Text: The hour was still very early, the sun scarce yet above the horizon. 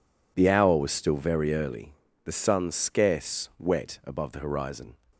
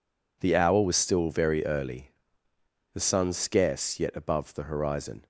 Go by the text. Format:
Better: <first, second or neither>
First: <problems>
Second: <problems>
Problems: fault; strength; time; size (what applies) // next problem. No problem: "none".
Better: second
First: says "wet" for "yet"; at 3.5 s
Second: none